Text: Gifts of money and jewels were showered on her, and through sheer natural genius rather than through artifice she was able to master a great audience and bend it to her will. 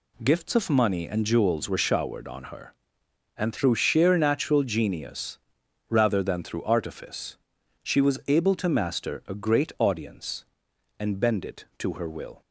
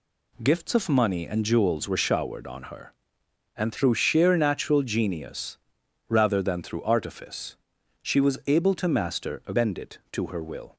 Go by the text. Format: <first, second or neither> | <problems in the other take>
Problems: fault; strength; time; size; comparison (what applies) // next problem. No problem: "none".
first | pauses between "genius" and "rather"; noticeable; at 5.5 s; 0.50 s long; noticeable in the first // pauses between "artifice" and "she"; noticeable; at 7.5 s; 0.46 s long; noticeable in the first // skips "great audience and"; at 9.5 s